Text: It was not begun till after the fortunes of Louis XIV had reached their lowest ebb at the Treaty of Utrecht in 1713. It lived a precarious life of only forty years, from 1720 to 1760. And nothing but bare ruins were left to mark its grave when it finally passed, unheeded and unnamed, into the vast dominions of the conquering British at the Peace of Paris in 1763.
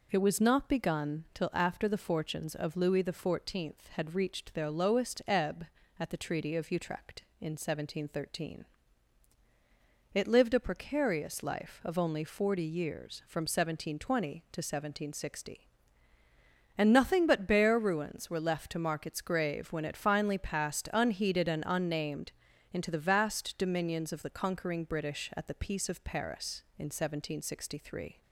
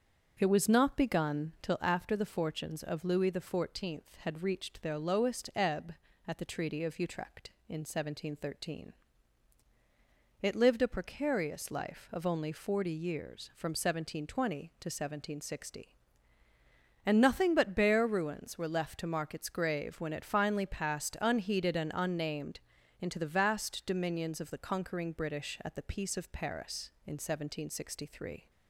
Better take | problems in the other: first | starts louder than the rest; until 2.0 s; 7 dB

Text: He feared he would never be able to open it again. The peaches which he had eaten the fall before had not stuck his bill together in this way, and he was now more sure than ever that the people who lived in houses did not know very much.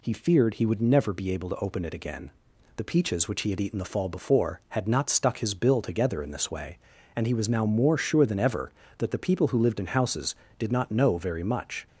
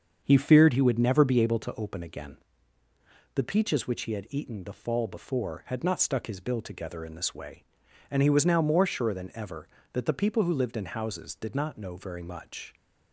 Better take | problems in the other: first | starts louder than the rest; strong; until 1.2 s; 7 dB // skips "it"; at 2.0 s

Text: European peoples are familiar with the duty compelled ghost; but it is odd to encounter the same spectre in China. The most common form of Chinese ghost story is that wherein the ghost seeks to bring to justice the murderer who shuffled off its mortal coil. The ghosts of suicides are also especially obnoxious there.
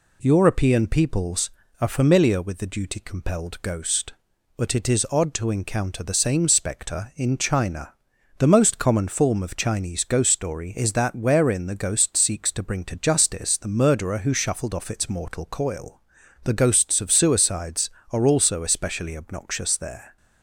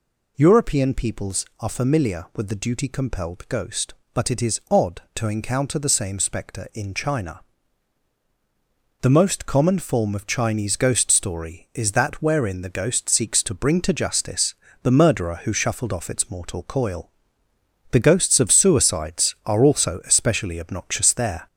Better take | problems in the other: first | gets louder; throughout; 3.5 dB // pauses between "justice" and "the"; slight; at 14.5 s; 0.28 s long

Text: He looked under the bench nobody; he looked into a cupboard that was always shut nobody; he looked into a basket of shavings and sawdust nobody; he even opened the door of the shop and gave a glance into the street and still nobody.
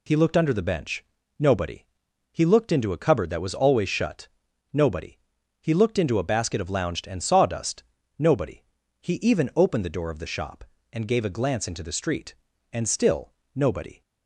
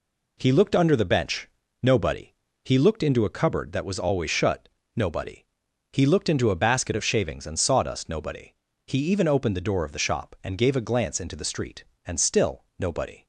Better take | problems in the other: second | pauses between "bench" and "nobody"; slight; at 1.0 s; 0.34 s long; slight in the second // pauses between "shut" and "nobody"; at 4.2 s; 0.42 s long; slight in the second // says "lounged" for "shavings"; at 6.6 s // pauses between "sawdust" and "nobody"; slight; at 7.8 s; 0.34 s long // pauses between "still" and "nobody"; slight; at 13.3 s; 0.20 s long; slight in the second

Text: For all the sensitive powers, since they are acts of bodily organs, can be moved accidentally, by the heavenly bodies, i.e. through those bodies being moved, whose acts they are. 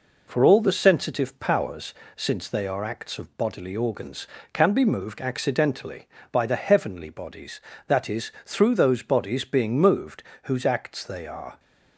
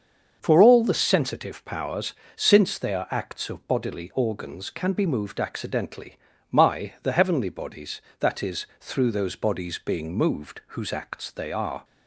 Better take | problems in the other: first | starts louder than the rest; until 1.4 s; 6.5 dB // says "my" for "by"; at 6.5 s

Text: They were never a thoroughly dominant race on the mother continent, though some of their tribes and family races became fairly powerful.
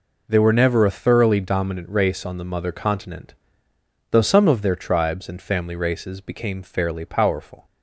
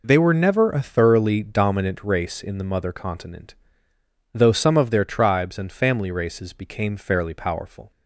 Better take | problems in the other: first | says "in" for "on"; at 2.4 s

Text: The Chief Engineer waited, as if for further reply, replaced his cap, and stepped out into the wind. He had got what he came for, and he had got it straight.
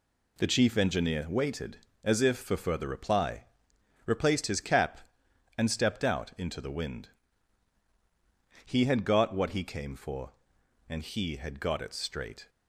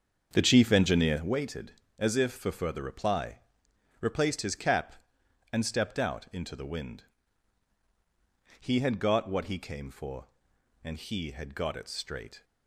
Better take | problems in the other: first | starts louder than the rest; until 1.3 s; 7 dB

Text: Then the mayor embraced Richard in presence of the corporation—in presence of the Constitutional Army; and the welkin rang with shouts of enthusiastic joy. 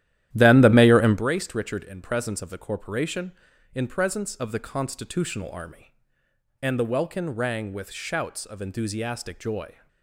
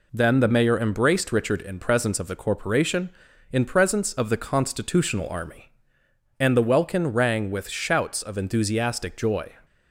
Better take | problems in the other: second | starts louder than the rest; strong; until 1.2 s; 12.5 dB

